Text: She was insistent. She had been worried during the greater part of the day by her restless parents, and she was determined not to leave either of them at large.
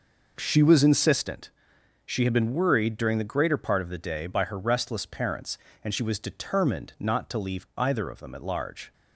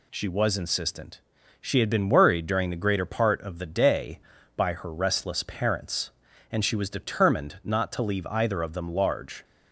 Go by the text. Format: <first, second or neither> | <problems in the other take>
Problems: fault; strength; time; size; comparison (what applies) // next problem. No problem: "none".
first | skips "at"; at 8.8 s